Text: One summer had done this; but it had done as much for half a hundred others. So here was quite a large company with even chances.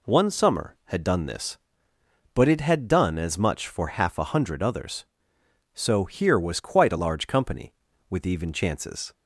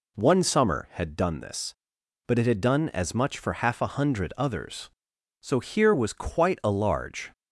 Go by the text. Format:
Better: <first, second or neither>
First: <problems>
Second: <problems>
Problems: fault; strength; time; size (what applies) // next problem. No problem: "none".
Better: first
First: none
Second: stops before "company with even chances"; at 7.3 s